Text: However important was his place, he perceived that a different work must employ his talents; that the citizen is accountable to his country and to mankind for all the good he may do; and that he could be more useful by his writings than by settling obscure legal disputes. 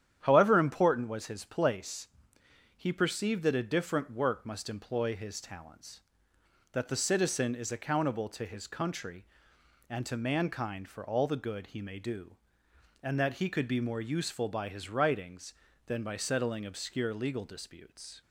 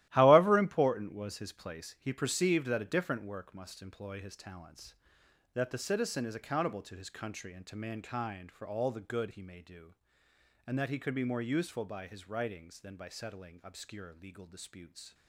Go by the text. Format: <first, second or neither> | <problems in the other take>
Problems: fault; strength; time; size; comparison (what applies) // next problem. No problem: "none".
first | gets quieter; strong; throughout; 11 dB // starts louder than the rest; strong; until 1.1 s; 15.5 dB; strong in the first